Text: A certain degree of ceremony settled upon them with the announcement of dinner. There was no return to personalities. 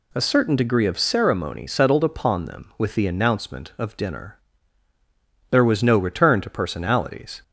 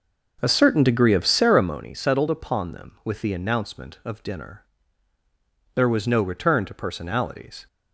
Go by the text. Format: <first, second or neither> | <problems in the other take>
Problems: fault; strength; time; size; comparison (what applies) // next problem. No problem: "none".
first | starts louder than the rest; noticeable; until 1.8 s; 6 dB